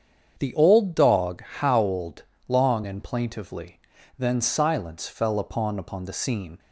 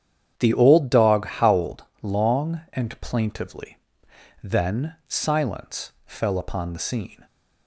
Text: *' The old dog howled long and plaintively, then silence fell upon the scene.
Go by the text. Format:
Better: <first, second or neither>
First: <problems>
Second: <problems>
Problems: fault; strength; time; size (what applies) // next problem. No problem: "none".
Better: second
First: starts louder than the rest; strong; until 1.3 s; 8 dB // pauses between "howled" and "long"; slight; at 2.2 s; 0.22 s long // says "upon" twice; at 5.7 s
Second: starts louder than the rest; strong; until 1.3 s; 9 dB // pauses between "howled" and "long"; slight; at 1.8 s; 0.18 s long